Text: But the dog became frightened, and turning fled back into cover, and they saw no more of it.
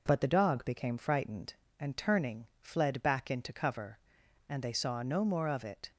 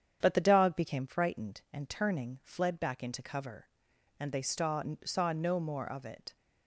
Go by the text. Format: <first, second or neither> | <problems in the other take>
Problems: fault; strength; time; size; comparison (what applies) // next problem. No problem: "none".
first | starts louder than the rest; strong; until 1.2 s; 8 dB // says "saw" twice; at 5.0 s